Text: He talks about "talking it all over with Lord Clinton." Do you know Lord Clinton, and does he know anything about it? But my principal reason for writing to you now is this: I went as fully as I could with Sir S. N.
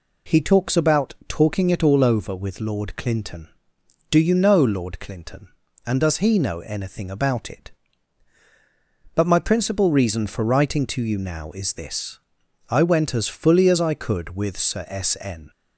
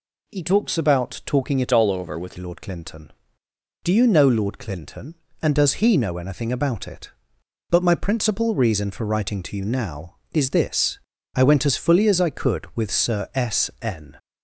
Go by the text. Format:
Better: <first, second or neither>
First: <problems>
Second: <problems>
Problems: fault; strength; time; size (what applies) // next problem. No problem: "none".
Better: first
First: none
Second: changes voice from "all" to "with"; from 1.7 to 2.3 s; 0.6 s long